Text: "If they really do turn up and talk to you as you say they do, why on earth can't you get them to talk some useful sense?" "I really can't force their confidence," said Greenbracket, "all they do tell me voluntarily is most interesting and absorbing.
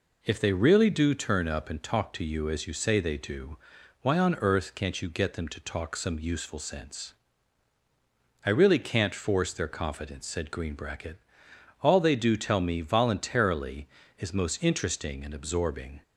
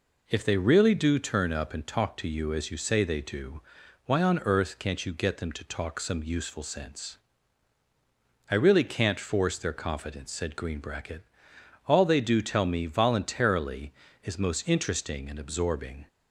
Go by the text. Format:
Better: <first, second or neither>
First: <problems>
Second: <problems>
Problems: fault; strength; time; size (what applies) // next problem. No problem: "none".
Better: neither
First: none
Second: none